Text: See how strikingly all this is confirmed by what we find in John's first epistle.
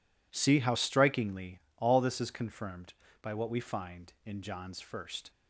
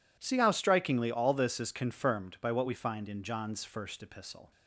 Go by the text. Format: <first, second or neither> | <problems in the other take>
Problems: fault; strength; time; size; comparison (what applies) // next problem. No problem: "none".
second | pauses between "strikingly" and "all"; slight; at 1.5 s; 0.18 s long // stops before "epistle"; at 5.3 s